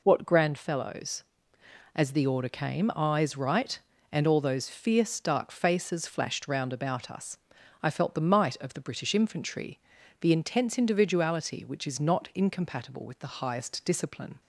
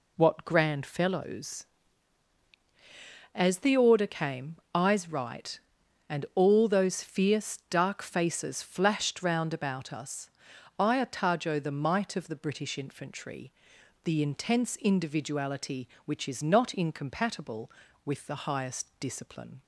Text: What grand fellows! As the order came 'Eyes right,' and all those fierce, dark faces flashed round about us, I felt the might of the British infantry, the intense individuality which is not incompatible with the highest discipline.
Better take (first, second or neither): first